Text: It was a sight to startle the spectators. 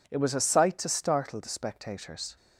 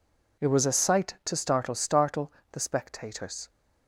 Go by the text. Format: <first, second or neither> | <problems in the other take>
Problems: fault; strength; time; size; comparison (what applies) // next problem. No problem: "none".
first | says "startle" twice; at 1.7 s